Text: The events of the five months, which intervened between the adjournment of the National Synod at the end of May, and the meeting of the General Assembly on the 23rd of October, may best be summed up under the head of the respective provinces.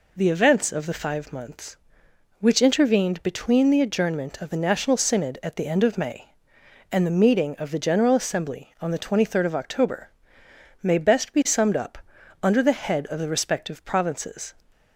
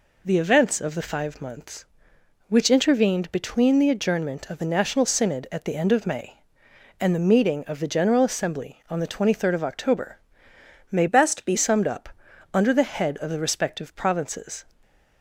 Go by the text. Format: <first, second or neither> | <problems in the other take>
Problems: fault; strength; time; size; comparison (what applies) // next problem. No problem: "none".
first | changes voice from "best" to "be"; from 11.0 to 11.5 s; 0.5 s long // pauses between "up" and "under"; noticeable; at 12.0 s; 0.46 s long; noticeable in the first